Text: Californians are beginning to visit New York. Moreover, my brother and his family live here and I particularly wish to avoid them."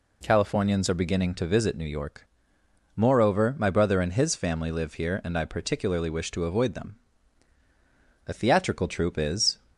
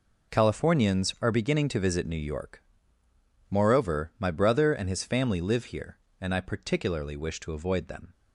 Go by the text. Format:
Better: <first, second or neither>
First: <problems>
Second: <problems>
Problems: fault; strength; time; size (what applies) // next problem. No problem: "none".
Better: second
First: goes on to say "A theatrical troupe is"; noticeable; from 8.2 s on; 1.3 s long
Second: none